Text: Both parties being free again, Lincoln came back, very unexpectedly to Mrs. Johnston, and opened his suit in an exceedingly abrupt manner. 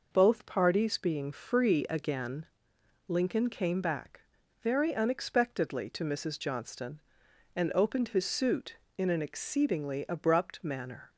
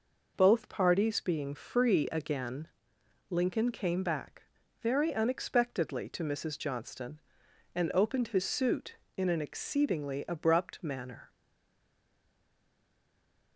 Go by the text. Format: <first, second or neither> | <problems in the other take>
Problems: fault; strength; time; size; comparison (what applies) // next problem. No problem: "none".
first | stays silent after the last word; from 11.2 s on; 2.3 s long